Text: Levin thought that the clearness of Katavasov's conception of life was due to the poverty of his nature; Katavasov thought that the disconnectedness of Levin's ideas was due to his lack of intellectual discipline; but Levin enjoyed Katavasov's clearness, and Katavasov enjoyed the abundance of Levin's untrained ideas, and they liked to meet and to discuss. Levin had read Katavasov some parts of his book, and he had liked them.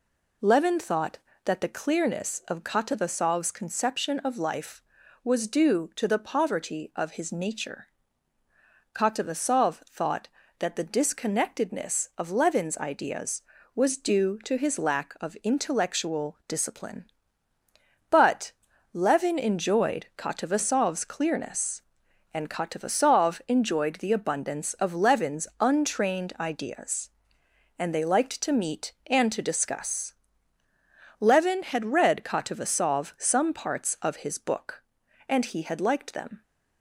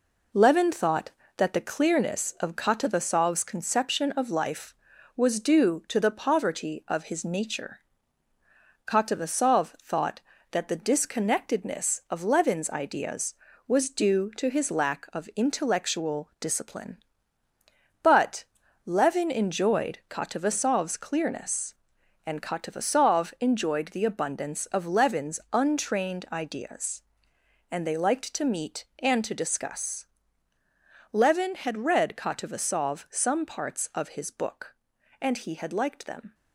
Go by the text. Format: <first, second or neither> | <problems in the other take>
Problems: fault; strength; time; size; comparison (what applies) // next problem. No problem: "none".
first | gets quieter; noticeable; throughout; 4.5 dB // pauses between "but" and "Levin"; at 18.4 s; 0.40 s long; also in the first